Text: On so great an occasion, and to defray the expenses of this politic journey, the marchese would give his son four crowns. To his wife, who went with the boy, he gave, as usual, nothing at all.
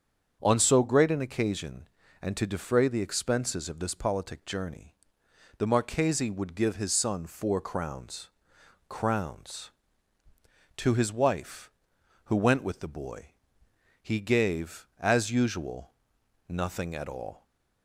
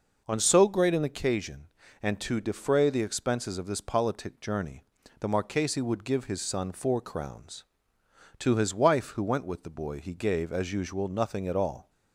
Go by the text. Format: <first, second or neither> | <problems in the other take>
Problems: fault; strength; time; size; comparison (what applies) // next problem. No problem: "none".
second | starts louder than the rest; until 1.4 s; 7 dB // says "crowns" twice; at 8.8 s